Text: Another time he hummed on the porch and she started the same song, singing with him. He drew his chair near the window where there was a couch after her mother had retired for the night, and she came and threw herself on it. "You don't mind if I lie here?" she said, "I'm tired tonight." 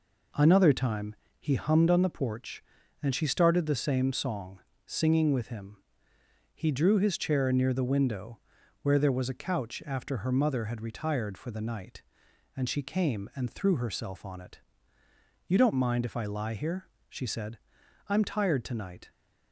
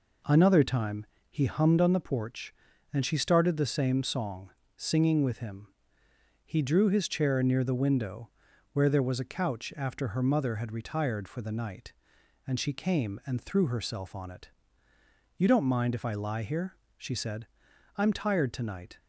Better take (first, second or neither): neither